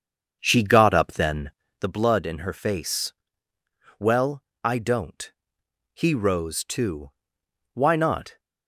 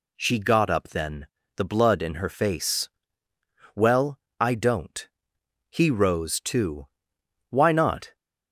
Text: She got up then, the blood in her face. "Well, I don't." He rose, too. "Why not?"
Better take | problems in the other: second | starts louder than the rest; strong; until 1.9 s; 7 dB

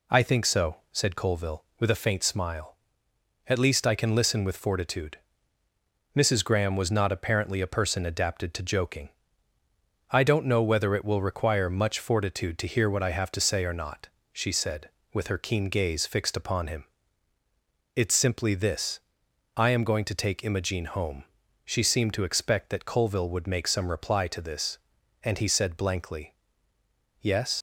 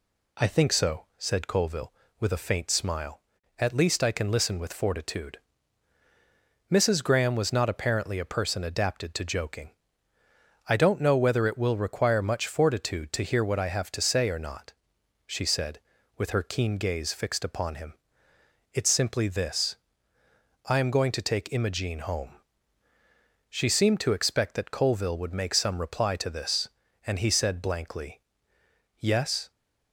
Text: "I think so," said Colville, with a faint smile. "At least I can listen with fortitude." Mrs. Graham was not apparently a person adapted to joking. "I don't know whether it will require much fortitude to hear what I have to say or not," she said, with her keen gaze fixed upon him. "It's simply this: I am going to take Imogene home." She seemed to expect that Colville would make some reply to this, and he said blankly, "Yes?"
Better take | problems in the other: second | leaves "Yes" unfinished; at 27.5 s; 100 ms

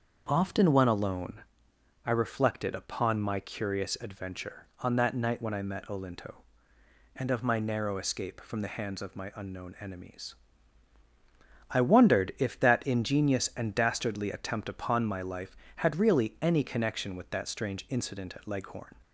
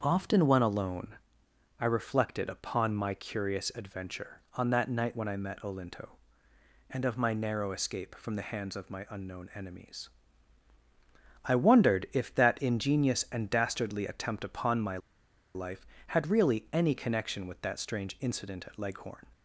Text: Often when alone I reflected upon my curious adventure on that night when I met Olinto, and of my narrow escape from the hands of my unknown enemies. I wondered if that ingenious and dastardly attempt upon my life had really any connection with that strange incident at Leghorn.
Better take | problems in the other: first | starts louder than the rest; until 1.0 s; 7 dB; also in the first // pauses between "alone" and "I"; noticeable; at 1.1 s; 0.66 s long; noticeable in the first // pauses between "my" and "life"; noticeable; at 14.9 s; 0.57 s long

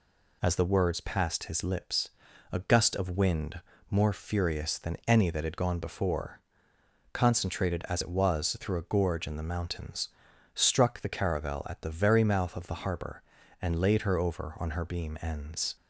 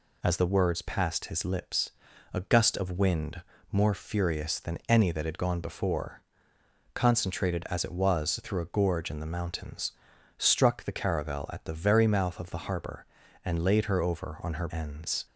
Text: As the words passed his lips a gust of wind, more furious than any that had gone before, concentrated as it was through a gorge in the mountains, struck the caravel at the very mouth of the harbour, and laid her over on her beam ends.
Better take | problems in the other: first | pauses between "lips" and "a"; at 1.9 s; 0.42 s long; also in the first // skips "beam"; at 14.6 s

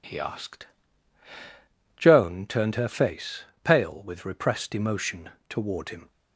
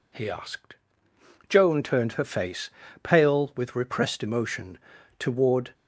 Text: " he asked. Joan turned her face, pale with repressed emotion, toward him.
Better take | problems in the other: first | stops before "him"; at 5.7 s

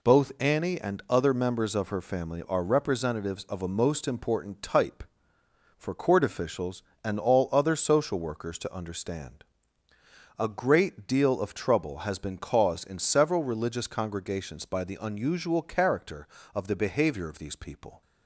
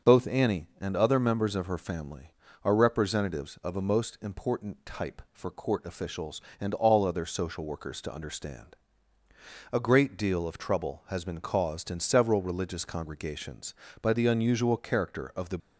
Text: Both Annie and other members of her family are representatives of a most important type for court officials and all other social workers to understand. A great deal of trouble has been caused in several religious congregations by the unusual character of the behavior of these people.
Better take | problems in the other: first | starts louder than the rest; until 1.1 s; 7 dB // stops before "behavior of these people"; at 15.6 s

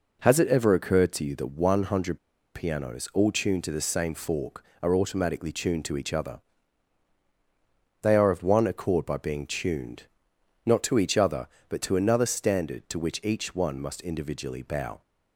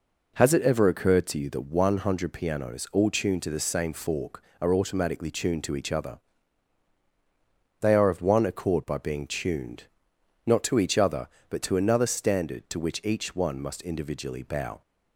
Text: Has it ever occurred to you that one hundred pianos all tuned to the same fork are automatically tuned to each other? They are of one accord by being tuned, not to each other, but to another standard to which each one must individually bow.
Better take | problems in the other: second | pauses between "hundred" and "pianos"; slight; at 2.1 s; 0.36 s long

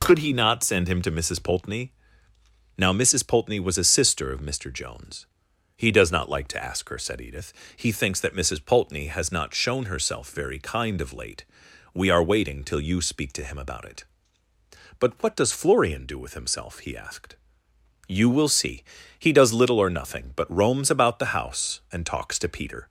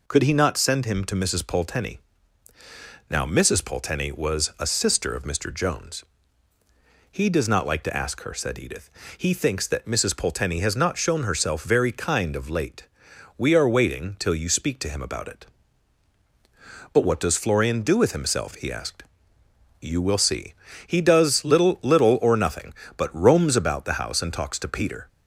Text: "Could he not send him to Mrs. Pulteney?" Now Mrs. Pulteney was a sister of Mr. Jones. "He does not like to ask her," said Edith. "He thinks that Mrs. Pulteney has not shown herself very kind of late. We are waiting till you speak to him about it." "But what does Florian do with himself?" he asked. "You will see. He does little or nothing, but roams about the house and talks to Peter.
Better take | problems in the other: first | says "little" twice; at 21.8 s

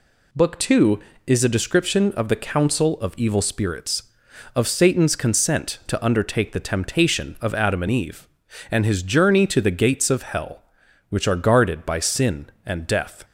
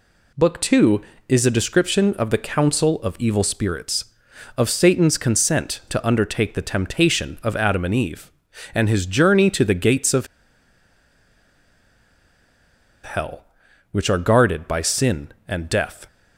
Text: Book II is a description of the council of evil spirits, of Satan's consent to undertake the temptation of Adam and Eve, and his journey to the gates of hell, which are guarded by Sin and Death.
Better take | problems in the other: first | pauses between "of" and "hell"; strong; at 10.2 s; 2.7 s long

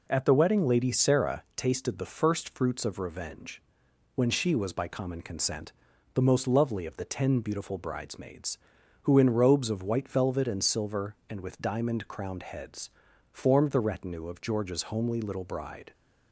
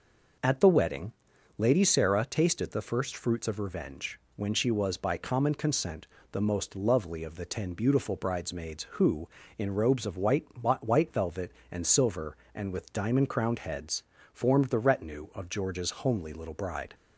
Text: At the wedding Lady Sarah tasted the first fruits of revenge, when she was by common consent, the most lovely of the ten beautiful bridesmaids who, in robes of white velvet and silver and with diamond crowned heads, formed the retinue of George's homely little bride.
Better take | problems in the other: first | pauses between "wedding" and "Lady"; noticeable; at 1.1 s; 0.46 s long // says "white" twice; at 10.6 s

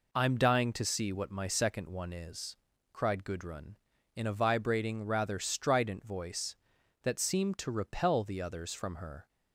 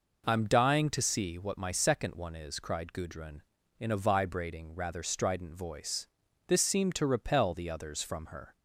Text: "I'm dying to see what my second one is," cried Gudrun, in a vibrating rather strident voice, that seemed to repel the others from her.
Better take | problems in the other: first | says "this" for "that"; at 6.4 s

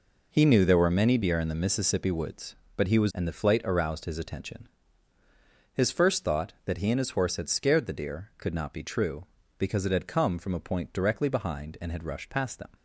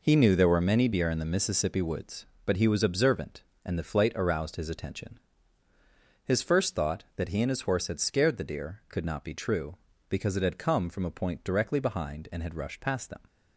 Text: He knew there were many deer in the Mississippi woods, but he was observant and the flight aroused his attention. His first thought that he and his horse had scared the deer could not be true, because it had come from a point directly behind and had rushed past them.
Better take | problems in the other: second | skips "observant"; at 3.1 s

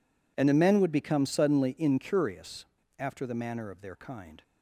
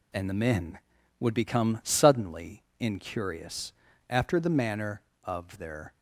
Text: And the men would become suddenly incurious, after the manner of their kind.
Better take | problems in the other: first | pauses between "suddenly" and "incurious"; slight; at 2.6 s; 0.16 s long // stops before "kind"; at 5.9 s

